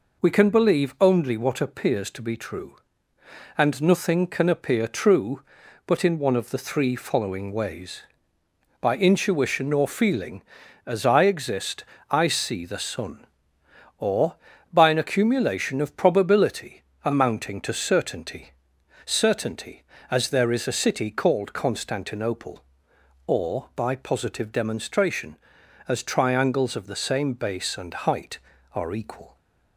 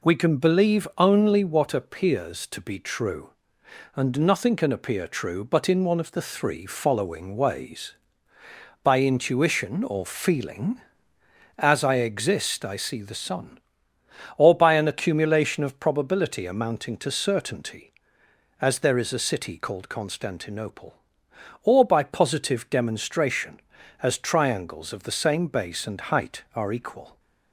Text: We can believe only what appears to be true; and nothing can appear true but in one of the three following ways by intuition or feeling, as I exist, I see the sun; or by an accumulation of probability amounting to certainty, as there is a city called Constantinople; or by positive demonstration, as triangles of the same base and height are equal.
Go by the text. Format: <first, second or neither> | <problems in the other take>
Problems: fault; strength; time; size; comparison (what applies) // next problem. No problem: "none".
second | pauses between "probability" and "amounting"; slight; at 16.8 s; 0.22 s long // says "certainty" twice; at 19.0 s // pauses between "and" and "height"; slight; at 27.9 s; 0.16 s long